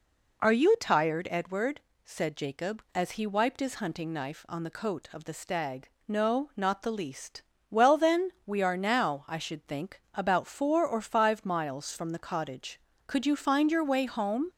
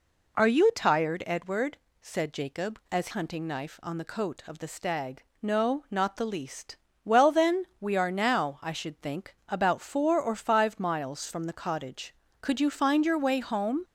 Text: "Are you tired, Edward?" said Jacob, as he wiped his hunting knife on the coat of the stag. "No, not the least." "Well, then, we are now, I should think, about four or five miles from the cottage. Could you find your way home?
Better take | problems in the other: first | skips "he wiped his"; at 3.0 s

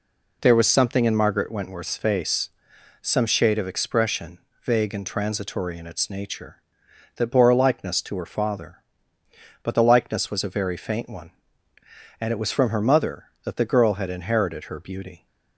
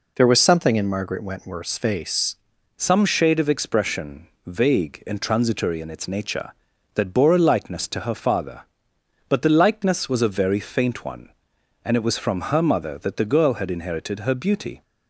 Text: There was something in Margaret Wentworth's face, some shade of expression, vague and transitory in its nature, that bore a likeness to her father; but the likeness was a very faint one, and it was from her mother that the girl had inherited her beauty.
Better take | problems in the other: first | changes voice at "some"; from 2.7 s on; 12.1 s long

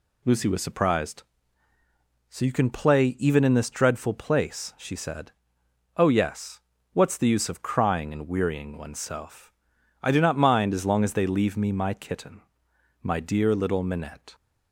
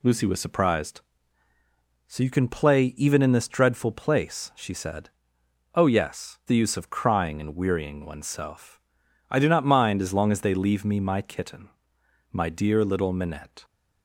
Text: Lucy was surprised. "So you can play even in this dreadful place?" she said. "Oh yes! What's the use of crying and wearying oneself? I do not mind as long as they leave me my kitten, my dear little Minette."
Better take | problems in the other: first | skips "What's"; at 6.4 s

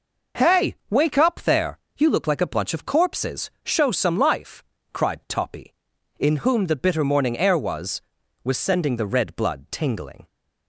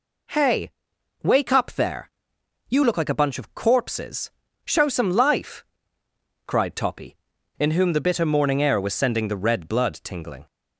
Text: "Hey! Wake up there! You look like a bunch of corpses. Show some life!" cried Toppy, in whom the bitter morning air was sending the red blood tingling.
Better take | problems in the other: second | says "was" twice; at 8.4 s

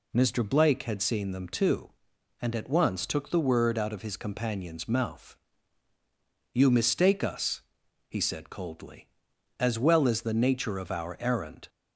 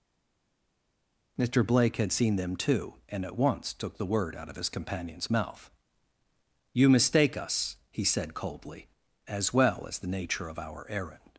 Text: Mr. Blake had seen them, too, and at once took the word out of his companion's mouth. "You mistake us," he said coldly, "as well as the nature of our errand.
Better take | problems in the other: first | stays silent before the first word; noticeable; until 1.3 s; 1.3 s long

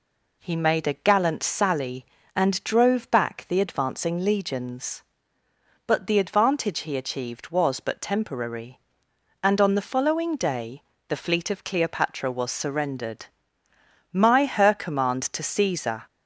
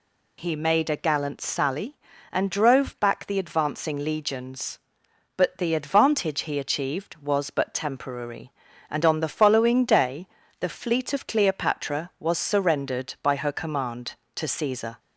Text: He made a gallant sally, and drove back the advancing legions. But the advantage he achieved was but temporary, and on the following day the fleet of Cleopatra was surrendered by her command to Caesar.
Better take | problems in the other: second | pauses between "day" and "the"; slight; at 10.8 s; 0.26 s long; slight in the second // says "my" for "by"; at 14.1 s

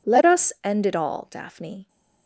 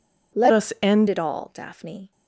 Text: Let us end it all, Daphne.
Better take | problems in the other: first | changes voice from "us" to "end"; from 0.5 to 1.0 s; 0.5 s long

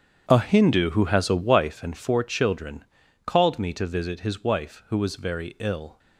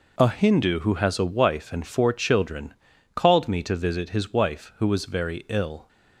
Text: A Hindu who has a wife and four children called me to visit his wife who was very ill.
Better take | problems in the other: second | starts louder than the rest; strong; until 1.8 s; 8.5 dB // pauses between "children" and "called"; at 2.8 s; 0.40 s long; also in the second

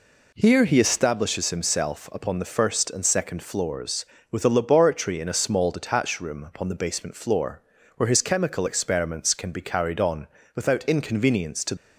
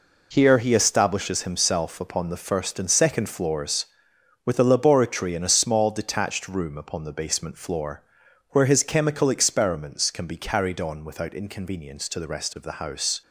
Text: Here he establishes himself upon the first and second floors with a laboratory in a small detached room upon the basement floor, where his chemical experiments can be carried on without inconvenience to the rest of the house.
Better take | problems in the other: second | pauses between "on" and "without"; slight; at 10.2 s; 0.28 s long // stops before "the rest of the house"; at 11.7 s

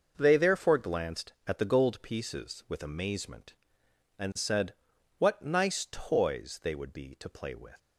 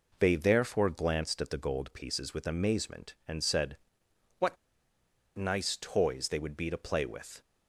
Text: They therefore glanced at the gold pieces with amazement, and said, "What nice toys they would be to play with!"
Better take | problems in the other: first | pauses between "What" and "nice"; noticeable; at 4.5 s; 0.82 s long

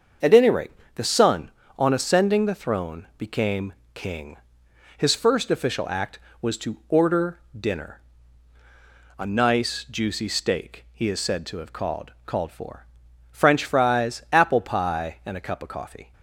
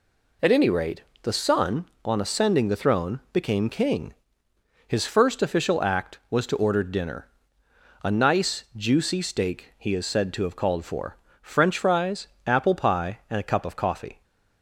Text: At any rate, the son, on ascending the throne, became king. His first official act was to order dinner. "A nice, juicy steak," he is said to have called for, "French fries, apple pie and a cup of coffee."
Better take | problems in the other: second | starts louder than the rest; until 1.4 s; 6.5 dB // pauses between "became" and "king"; slight; at 3.7 s; 0.22 s long // pauses between "order" and "dinner"; slight; at 7.3 s; 0.20 s long // says "called" twice; at 12.2 s

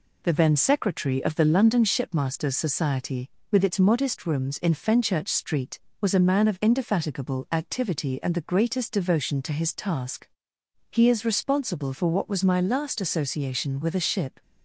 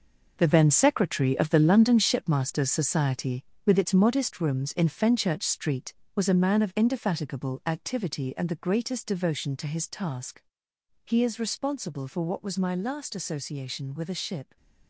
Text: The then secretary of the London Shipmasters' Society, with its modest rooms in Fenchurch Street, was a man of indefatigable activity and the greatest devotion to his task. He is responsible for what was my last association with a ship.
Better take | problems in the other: first | gets quieter; strong; throughout; 10.5 dB

